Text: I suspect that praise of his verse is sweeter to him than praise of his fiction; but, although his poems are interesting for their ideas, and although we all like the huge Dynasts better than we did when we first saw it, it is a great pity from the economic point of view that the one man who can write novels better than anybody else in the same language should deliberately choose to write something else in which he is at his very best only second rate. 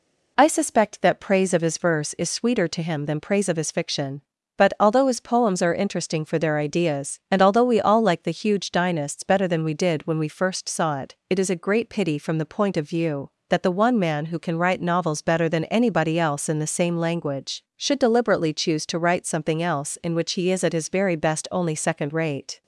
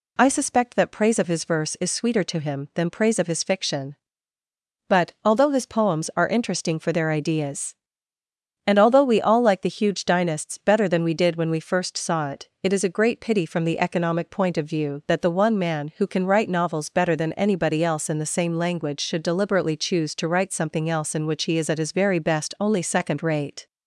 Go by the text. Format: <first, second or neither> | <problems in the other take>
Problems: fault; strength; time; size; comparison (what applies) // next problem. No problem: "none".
second | skips "economic"; at 12.4 s